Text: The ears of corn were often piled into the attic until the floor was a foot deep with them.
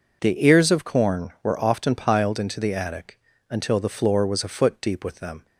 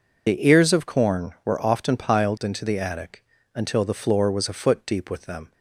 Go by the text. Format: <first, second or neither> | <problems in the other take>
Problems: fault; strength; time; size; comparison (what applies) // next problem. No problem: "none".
first | loses the start of "The"; at 0.2 s; 40 ms // pauses between "attic" and "until"; slight; at 3.2 s; 0.32 s long; slight in the first